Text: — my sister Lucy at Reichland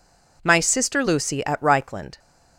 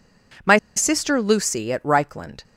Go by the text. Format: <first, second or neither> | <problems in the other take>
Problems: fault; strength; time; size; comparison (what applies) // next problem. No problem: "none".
first | pauses between "my" and "sister"; slight; at 0.5 s; 0.20 s long